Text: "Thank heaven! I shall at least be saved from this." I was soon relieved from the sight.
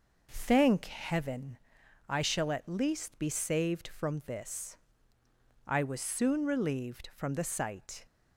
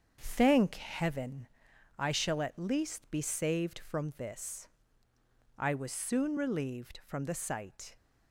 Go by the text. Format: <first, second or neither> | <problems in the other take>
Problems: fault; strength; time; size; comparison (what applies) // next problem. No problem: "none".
first | gets quieter; noticeable; throughout; 5.5 dB